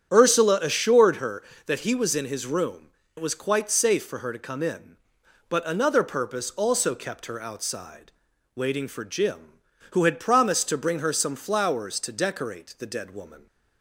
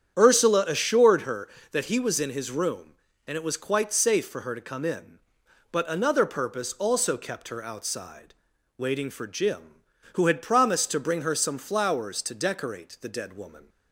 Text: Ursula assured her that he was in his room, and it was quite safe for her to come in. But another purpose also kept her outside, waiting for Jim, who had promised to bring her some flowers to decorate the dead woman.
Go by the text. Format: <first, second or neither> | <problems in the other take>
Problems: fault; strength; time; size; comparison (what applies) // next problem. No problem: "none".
second | starts louder than the rest; strong; until 1.1 s; 8.5 dB; strong in the second // skips "and"; at 3.0 s